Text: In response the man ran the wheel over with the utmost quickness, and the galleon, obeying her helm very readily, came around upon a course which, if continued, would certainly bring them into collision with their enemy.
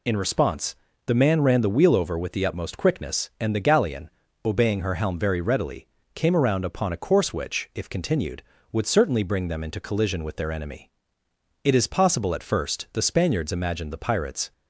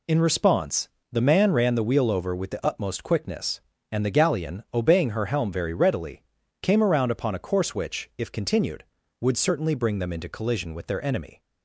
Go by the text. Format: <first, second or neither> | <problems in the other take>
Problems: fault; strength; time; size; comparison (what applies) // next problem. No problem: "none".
second | pauses between "response" and "the"; slight; at 0.7 s; 0.30 s long; slight in the second // goes on to say "It is possible at first the Spaniards imagined the pirates"; strong; from 11.6 s on; 2.8 s long